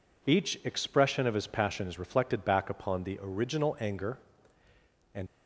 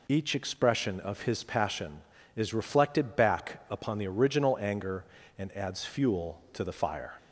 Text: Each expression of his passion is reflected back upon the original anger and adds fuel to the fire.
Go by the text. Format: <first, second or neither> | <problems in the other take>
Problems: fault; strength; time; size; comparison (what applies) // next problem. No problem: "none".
second | stops before "adds fuel to the fire"; at 5.2 s